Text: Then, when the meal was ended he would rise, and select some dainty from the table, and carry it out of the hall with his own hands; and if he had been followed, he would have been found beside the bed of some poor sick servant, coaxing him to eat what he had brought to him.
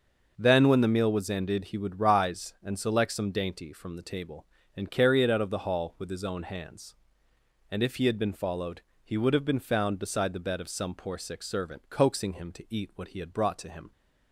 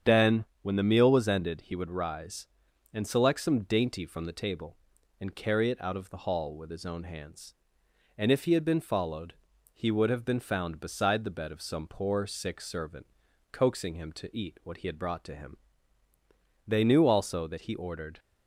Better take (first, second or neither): first